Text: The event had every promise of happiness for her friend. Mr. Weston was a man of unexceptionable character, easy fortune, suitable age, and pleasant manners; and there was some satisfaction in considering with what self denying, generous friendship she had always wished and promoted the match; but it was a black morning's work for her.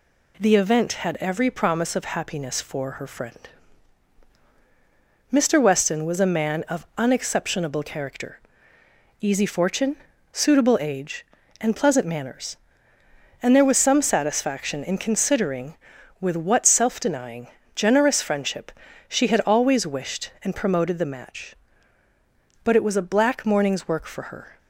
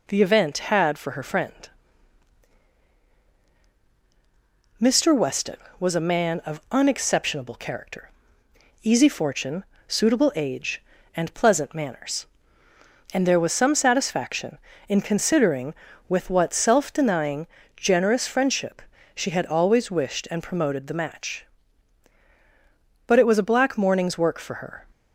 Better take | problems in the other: first | skips "every promise of happiness"; at 0.9 s // pauses between "friendship" and "she"; slight; at 18.8 s; 0.32 s long; slight in the first

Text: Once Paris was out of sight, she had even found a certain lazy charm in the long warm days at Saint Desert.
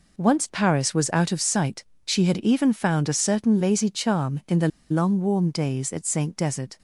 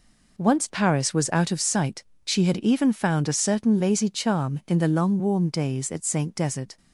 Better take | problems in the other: second | pauses between "the" and "long"; slight; at 4.6 s; 0.22 s long

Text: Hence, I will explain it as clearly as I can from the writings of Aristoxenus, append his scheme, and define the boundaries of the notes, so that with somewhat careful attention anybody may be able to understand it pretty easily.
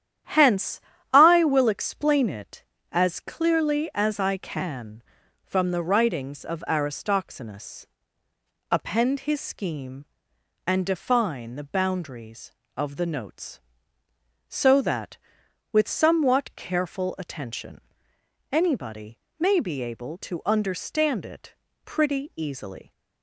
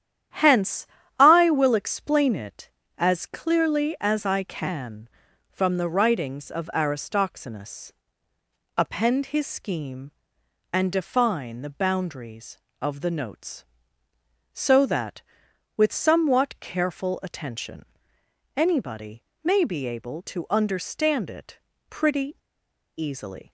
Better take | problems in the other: first | starts louder than the rest; strong; until 1.6 s; 10 dB; strong in the first // pauses between "attention" and "anybody"; noticeable; at 17.8 s; 0.72 s long; noticeable in the first // pauses between "anybody" and "may"; slight; at 19.2 s; 0.22 s long; slight in the first // pauses between "it" and "pretty"; slight; at 21.5 s; 0.30 s long; slight in the first // pauses between "pretty" and "easily"; noticeable; at 22.3 s; 0.59 s long

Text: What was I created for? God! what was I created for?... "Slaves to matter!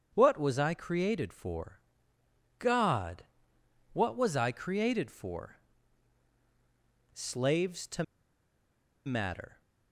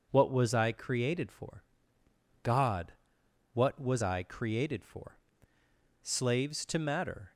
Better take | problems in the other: second | starts louder than the rest; strong; until 1.1 s; 7.5 dB // pauses between "to" and "matter"; at 8.0 s; 1.0 s long

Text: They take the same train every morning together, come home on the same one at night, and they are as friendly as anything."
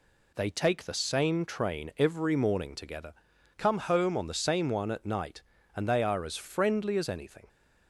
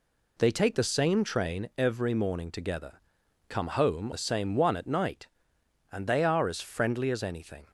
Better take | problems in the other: first | skips "on"; at 4.1 s

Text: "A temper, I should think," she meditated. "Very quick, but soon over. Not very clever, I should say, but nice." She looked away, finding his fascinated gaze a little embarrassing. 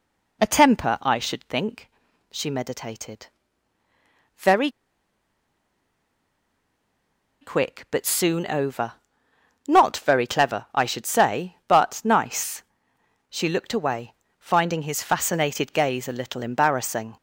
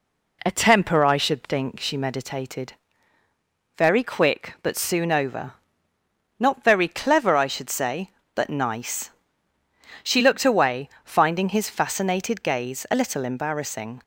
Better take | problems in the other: second | pauses between "Very" and "quick"; strong; at 4.6 s; 2.7 s long

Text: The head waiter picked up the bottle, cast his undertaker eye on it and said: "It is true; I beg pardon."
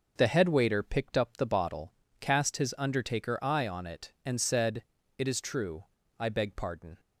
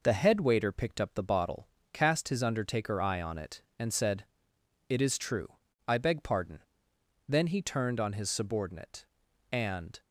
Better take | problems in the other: first | goes on to say "Then he turned on his subordinate and"; strong; from 7.2 s on; 2.7 s long

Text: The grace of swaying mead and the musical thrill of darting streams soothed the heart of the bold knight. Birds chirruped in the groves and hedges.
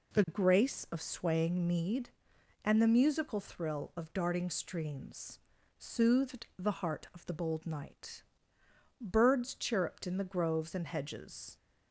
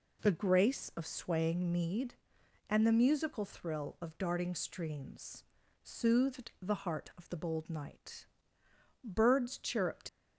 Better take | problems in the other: first | pauses between "streams" and "soothed"; at 5.4 s; 0.38 s long; also in the first // stops before "in the groves and hedges"; at 10.0 s

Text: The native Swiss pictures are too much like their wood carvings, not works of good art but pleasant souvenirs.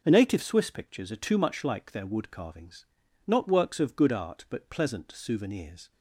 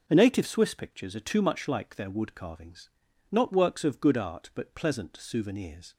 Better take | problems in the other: neither | none

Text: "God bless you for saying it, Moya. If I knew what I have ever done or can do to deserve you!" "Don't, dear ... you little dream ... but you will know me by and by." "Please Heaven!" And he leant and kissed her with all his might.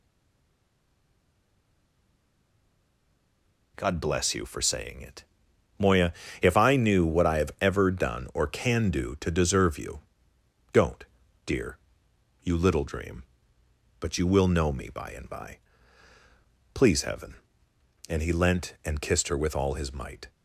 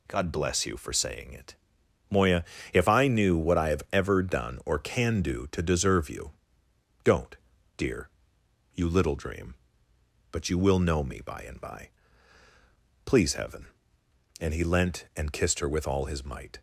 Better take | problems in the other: second | stays silent before the first word; strong; until 3.7 s; 3.7 s long

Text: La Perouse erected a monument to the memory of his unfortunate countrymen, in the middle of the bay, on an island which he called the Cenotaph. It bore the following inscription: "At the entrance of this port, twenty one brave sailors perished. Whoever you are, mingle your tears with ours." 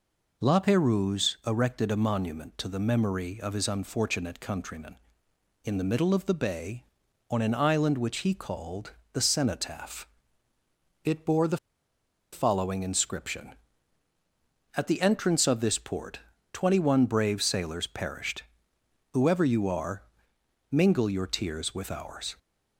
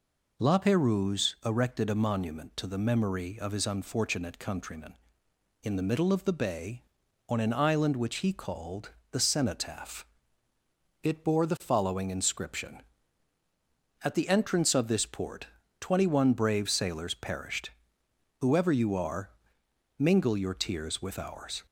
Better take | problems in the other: second | pauses between "called" and "the"; slight; at 8.9 s; 0.22 s long; slight in the second // pauses between "the" and "following"; noticeable; at 11.5 s; 0.76 s long

